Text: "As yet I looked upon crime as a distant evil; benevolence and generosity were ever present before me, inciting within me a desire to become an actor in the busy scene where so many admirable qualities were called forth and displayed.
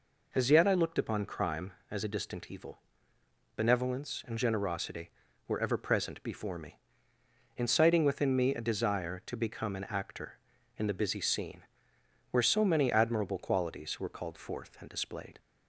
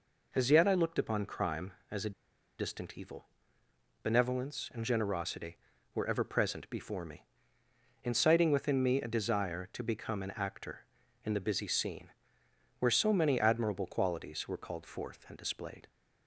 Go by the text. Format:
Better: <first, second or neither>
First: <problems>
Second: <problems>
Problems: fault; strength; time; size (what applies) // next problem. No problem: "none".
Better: first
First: pauses between "scene" and "where"; noticeable; at 11.6 s; 0.66 s long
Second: pauses between "a" and "distant"; noticeable; at 2.1 s; 0.47 s long // pauses between "scene" and "where"; noticeable; at 12.1 s; 0.68 s long